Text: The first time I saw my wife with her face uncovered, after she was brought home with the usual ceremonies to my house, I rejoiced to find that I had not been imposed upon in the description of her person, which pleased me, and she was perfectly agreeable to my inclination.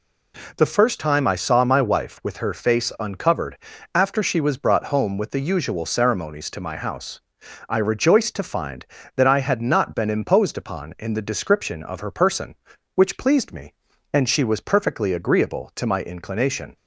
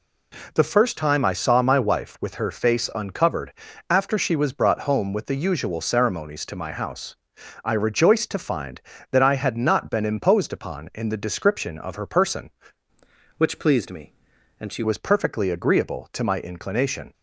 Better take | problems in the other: first | changes voice from "which" to "she"; from 13.3 to 14.8 s; 1.5 s long

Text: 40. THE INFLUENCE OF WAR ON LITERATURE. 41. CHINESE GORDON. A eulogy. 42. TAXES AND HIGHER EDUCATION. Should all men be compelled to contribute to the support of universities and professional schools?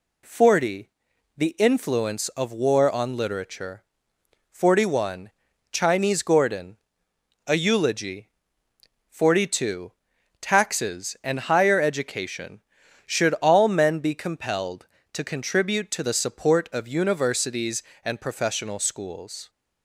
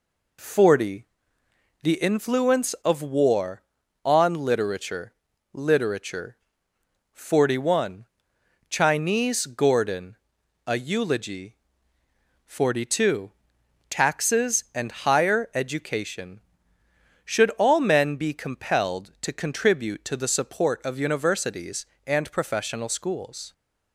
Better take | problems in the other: first | says "LITERATURE" twice; at 5.5 s

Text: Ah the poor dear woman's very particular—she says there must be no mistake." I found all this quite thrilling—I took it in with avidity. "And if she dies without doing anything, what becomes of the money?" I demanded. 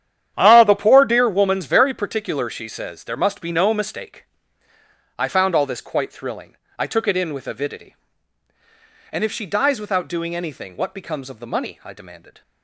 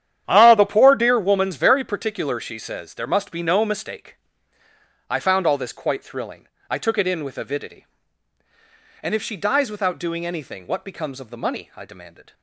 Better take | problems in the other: neither | starts louder than the rest; strong; the same in both

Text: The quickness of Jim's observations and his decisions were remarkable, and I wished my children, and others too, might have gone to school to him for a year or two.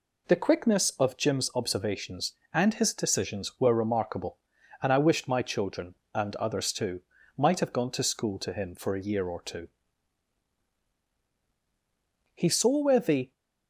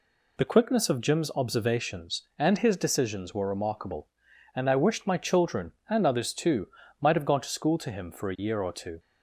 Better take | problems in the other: second | goes on to say "He saw where the"; noticeable; from 12.3 s on; 0.96 s long

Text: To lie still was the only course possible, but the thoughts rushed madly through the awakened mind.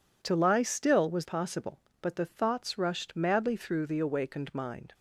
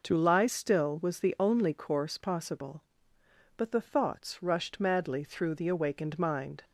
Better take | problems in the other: second | skips "the only course"; at 1.2 s

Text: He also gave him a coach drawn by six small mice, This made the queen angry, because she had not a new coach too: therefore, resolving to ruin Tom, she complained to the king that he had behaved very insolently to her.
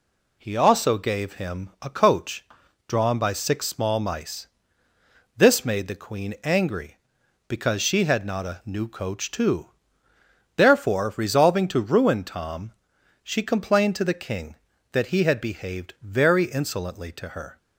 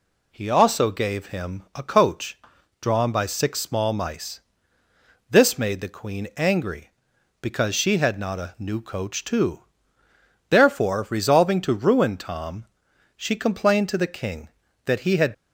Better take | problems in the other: first | pauses between "coach" and "drawn"; at 2.3 s; 0.42 s long; also in the first // stops before "behaved very insolently to her"; at 15.3 s

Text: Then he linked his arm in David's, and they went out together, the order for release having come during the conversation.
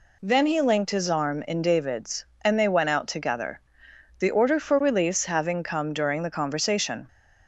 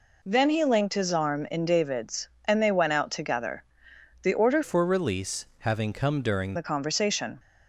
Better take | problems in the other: first | changes voice from "for" to "during"; from 4.6 to 6.5 s; 1.9 s long

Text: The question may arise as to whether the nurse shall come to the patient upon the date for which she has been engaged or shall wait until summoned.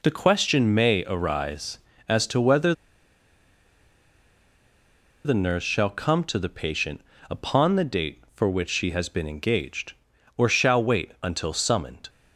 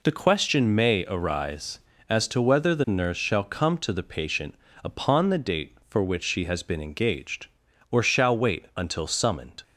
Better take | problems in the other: second | pauses between "whether" and "the"; strong; at 2.7 s; 2.5 s long // pauses between "patient" and "upon"; slight; at 7.0 s; 0.30 s long; slight in the second

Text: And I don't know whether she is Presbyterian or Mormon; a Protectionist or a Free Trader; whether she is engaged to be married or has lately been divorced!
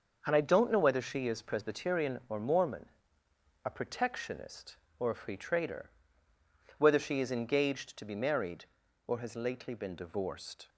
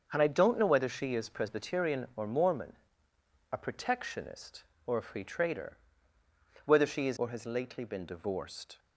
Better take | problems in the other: first | starts louder than the rest; until 1.1 s; 6.5 dB; also in the first // skips "engaged to be married"; at 7.1 s

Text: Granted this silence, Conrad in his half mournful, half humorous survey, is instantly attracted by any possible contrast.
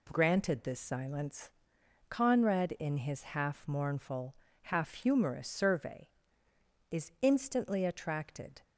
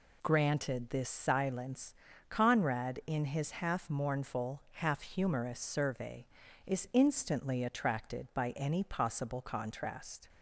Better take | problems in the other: second | stops before "by any possible contrast"; at 8.6 s

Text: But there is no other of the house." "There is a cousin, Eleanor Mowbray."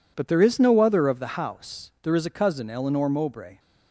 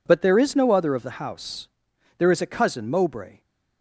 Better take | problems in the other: first | skips "Eleanor"; at 2.8 s

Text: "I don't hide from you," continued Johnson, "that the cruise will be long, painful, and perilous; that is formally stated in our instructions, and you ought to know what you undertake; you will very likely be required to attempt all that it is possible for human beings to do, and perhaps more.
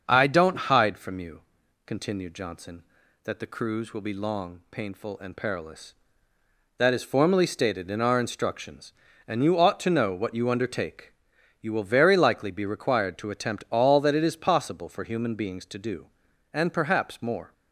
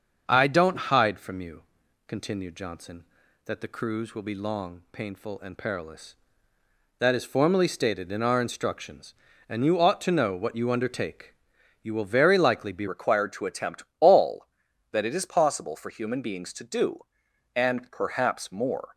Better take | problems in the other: first | starts louder than the rest; until 1.3 s; 6.5 dB; also in the first // changes voice at "required"; from 12.8 s on; 6.1 s long // pauses between "attempt" and "all"; slight; at 13.8 s; 0.16 s long

